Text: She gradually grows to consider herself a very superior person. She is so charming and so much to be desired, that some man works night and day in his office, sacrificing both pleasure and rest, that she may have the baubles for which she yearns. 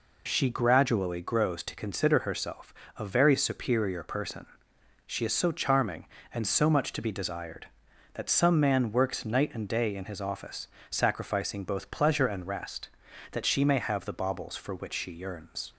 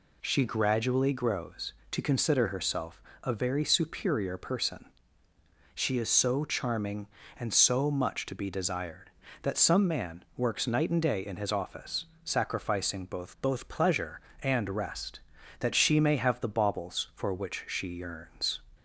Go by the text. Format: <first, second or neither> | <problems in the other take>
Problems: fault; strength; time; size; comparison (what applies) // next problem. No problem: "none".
first | pauses between "herself" and "a"; slight; at 3.0 s; 0.22 s long; slight in the first // says "both" twice; at 13.3 s